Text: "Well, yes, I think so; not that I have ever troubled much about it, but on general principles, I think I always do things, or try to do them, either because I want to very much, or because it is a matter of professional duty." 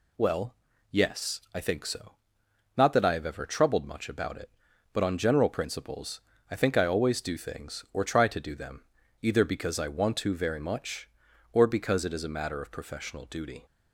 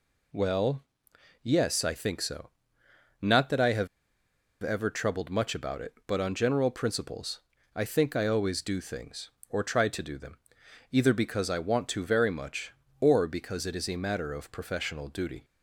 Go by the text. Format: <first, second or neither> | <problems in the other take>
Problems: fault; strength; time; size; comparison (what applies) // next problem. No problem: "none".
first | pauses between "have" and "ever"; noticeable; at 3.8 s; 0.74 s long